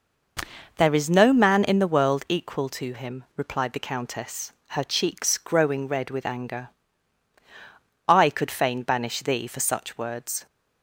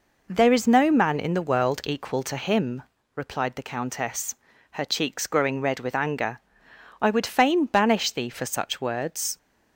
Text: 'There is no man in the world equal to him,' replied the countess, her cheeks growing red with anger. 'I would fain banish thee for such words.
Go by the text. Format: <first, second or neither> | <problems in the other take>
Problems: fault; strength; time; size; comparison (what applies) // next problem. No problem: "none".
second | says "could" for "would"; at 8.2 s